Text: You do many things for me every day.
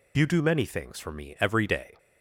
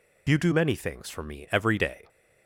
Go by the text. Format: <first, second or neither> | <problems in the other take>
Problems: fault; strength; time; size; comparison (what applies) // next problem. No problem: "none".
neither | none